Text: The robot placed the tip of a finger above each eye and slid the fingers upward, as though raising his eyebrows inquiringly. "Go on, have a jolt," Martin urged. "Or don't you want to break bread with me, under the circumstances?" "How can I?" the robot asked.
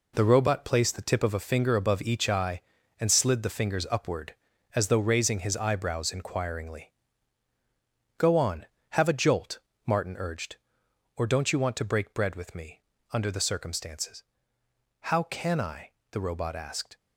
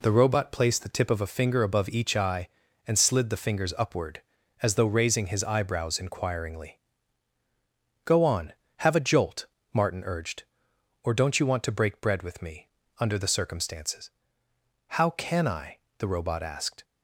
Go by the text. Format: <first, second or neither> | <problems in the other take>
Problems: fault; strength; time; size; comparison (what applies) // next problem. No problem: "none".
second | gets quieter; strong; throughout; 8 dB